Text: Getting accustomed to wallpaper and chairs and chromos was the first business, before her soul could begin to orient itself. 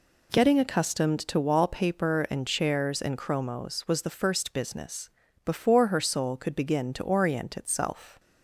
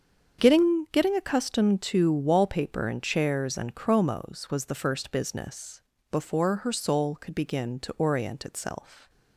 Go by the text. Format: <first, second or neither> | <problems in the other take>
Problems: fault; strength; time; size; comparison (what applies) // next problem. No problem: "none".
first | starts louder than the rest; until 1.4 s; 7 dB // says "Getting" twice; at 0.9 s